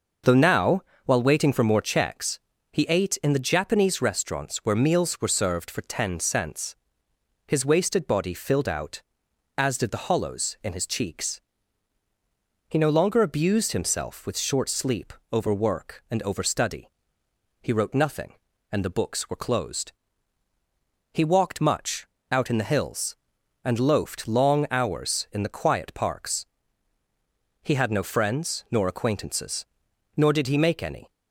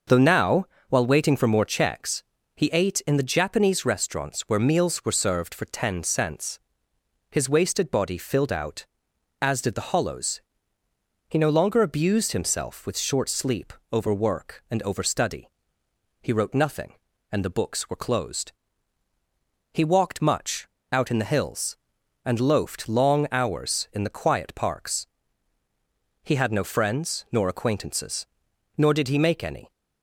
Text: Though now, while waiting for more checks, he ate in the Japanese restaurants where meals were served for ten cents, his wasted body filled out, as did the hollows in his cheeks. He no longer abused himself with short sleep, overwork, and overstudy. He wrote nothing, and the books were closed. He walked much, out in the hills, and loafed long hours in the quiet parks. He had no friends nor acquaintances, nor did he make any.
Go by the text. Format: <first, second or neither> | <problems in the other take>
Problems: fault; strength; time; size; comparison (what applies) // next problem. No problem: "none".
first | starts louder than the rest; noticeable; until 1.3 s; 6 dB // skips "in his cheeks"; at 10.8 s